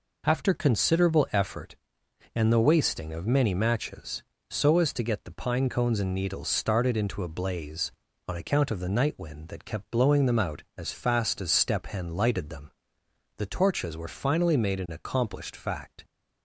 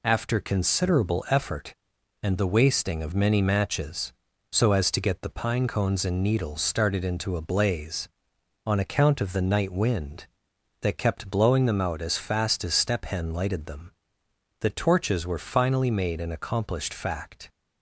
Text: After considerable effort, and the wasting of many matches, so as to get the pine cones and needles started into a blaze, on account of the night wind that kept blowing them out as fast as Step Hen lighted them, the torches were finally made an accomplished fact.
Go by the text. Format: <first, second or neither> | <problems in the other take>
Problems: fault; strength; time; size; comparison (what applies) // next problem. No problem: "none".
neither | none